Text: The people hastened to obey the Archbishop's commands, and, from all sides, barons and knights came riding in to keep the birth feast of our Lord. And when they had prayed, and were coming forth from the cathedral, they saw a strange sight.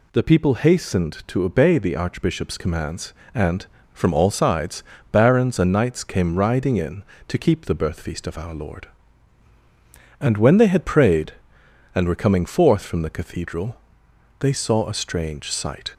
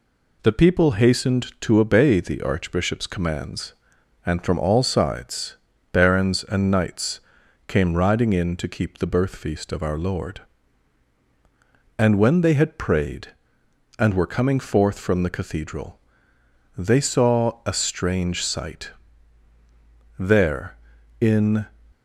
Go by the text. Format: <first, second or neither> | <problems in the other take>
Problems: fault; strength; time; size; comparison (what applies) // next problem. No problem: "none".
first | pauses between "knights" and "came"; noticeable; at 7.2 s; 0.46 s long // goes on to say "There in"; from 20.1 s on; 1.4 s long